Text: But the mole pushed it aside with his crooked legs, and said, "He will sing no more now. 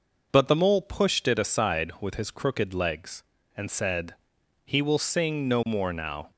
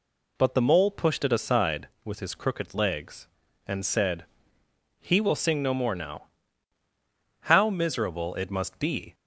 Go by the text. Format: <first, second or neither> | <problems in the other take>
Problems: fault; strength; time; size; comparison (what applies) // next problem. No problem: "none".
first | goes on to say "How miserable it must be"; strong; from 7.4 s on; 1.7 s long